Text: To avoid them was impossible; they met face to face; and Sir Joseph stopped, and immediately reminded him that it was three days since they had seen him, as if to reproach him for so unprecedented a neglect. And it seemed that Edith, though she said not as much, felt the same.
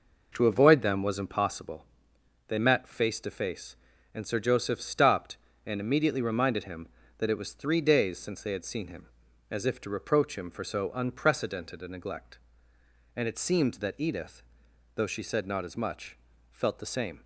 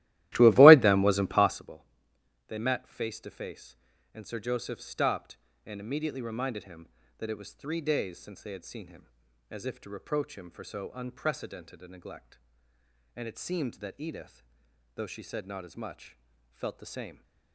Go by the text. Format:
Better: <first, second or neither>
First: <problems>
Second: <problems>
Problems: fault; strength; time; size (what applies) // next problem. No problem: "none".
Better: first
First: none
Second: starts louder than the rest; strong; until 1.7 s; 15.5 dB